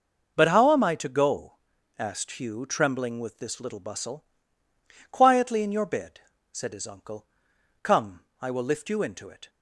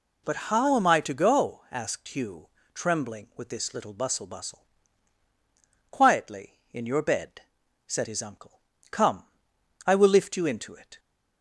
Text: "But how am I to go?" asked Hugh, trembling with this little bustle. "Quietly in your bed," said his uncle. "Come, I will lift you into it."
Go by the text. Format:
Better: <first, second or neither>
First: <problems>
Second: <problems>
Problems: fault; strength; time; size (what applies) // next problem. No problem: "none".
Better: first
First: none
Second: says "bustle" twice; at 4.2 s